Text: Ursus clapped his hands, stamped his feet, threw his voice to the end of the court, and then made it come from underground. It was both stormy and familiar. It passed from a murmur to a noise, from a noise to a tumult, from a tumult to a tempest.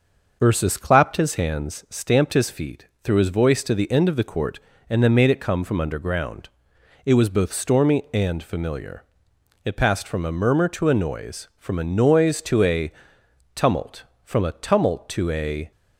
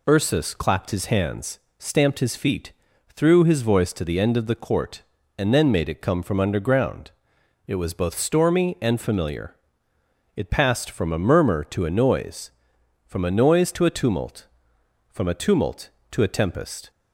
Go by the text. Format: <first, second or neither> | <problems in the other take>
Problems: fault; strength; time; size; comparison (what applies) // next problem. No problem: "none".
second | starts louder than the rest; noticeable; until 1.4 s; 6 dB // pauses between "a" and "tumult"; noticeable; at 12.9 s; 0.62 s long // stops before "tempest"; at 15.7 s